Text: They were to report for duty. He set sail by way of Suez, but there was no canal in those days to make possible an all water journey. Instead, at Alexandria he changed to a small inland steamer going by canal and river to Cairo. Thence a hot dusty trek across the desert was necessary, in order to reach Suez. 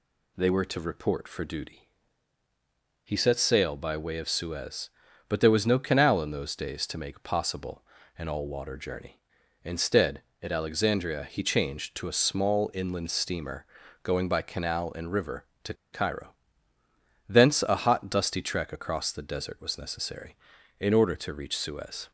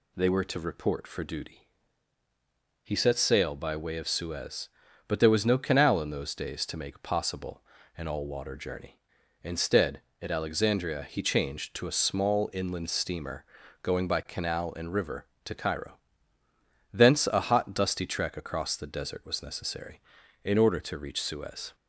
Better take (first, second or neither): second